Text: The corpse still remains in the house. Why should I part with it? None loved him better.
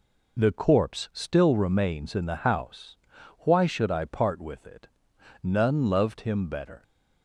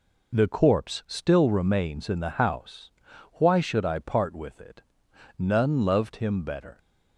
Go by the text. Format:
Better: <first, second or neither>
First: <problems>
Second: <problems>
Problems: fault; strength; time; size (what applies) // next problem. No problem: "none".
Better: neither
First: none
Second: none